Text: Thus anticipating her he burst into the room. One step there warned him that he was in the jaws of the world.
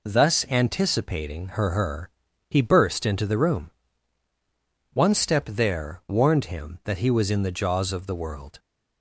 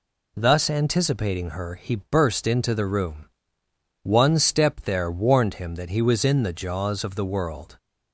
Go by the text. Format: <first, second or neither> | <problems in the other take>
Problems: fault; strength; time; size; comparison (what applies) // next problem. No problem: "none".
second | says "her" twice; at 1.7 s